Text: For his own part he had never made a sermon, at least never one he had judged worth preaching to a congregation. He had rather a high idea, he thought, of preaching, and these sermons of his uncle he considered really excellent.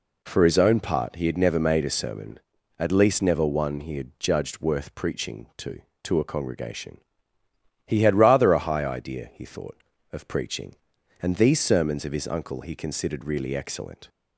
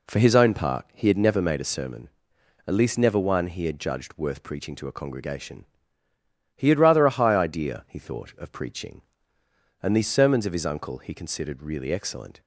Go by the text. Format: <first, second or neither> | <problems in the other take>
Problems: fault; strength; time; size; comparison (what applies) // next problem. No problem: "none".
second | says "to" twice; at 6.0 s